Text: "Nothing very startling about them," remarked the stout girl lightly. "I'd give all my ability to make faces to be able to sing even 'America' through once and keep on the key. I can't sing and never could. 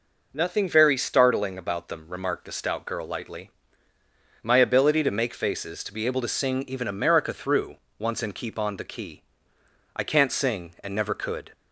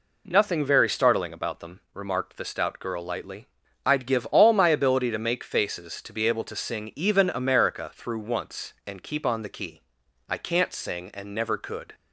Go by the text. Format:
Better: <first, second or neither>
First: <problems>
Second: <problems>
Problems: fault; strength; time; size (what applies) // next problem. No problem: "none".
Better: second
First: skips "I'd give all"; at 3.9 s // pauses between "through" and "once"; slight; at 7.7 s; 0.20 s long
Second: none